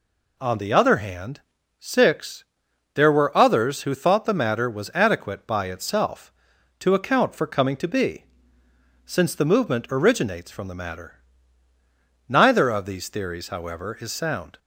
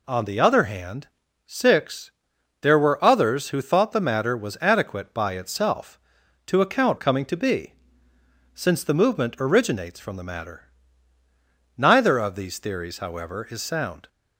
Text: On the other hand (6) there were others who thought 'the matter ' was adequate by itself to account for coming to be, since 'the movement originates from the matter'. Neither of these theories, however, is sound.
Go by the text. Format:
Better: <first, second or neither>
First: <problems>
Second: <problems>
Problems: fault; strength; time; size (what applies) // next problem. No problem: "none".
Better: first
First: none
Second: skips "for"; at 6.9 s